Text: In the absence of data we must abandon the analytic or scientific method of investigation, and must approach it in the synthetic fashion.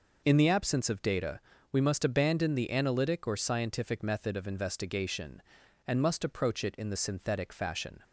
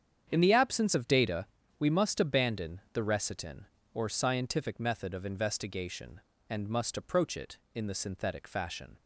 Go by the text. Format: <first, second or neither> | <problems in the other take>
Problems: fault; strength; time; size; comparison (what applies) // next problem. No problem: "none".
first | starts louder than the rest; strong; until 1.3 s; 8.5 dB // pauses between "data" and "we"; slight; at 1.4 s; 0.32 s long; slight in the first // says "recitin" for "analytic"; at 3.0 s